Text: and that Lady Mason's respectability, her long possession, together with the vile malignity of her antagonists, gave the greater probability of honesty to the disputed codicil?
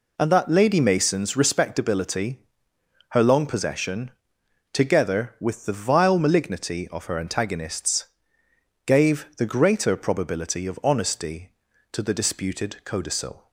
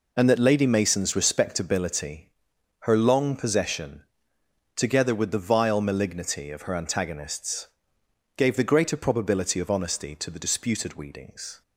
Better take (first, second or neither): first